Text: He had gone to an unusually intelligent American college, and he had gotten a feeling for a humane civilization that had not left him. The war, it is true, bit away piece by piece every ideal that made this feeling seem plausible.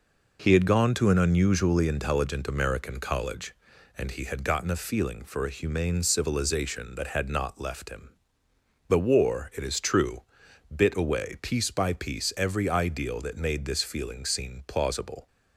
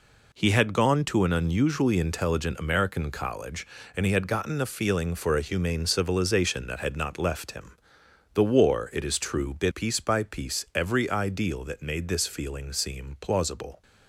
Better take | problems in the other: first | skips "away"; at 9.7 s

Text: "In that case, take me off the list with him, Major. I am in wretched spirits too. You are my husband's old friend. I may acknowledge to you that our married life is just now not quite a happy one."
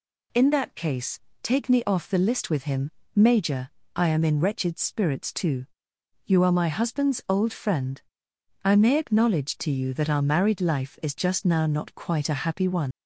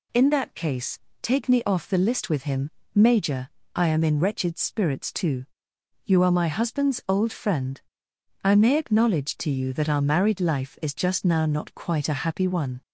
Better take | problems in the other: second | leaves "one" unfinished; at 12.9 s; 110 ms

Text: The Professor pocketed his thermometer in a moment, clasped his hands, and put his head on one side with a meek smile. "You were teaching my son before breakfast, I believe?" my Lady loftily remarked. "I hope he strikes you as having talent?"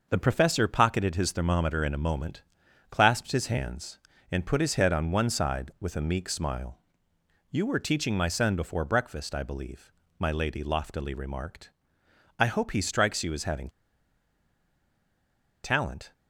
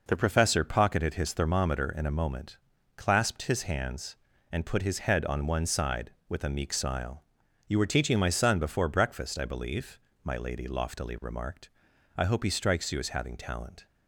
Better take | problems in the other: second | pauses between "having" and "talent"; strong; at 13.6 s; 1.9 s long

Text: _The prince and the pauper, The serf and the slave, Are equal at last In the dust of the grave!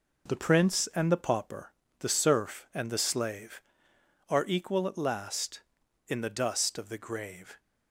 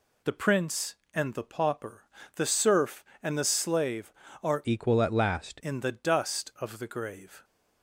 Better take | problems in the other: first | changes voice from "equal" to "last"; from 4.6 to 5.6 s; 1.0 s long

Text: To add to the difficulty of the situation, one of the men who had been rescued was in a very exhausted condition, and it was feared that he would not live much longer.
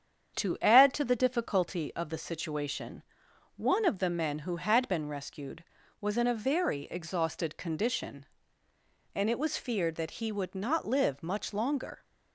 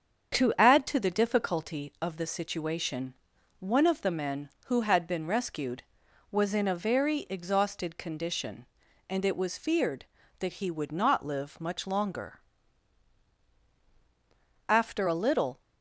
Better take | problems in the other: first | starts louder than the rest; strong; until 1.4 s; 7.5 dB; strong in the first // goes on to say "After a little"; noticeable; from 14.6 s on; 0.90 s long

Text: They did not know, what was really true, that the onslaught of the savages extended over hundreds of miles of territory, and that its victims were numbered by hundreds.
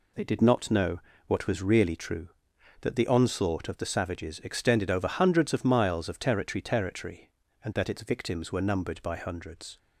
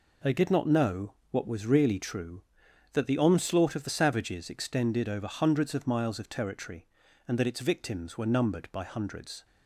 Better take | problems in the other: second | says "territory" twice; at 6.6 s

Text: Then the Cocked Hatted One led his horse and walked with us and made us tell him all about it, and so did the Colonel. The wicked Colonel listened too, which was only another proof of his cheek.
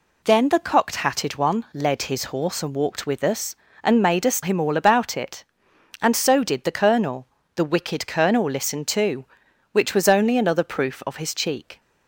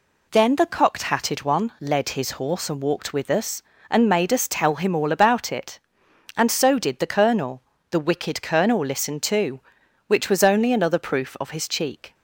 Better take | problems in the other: second | skips "tell"; at 4.4 s

